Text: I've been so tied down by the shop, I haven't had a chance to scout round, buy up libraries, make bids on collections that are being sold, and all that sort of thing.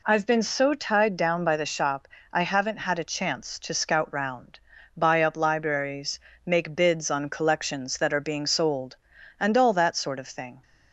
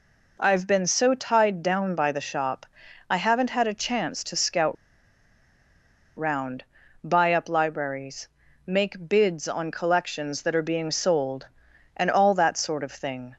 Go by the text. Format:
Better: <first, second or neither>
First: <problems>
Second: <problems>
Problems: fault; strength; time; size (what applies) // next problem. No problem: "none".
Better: first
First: none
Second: pauses between "scout" and "round"; strong; at 4.7 s; 1.4 s long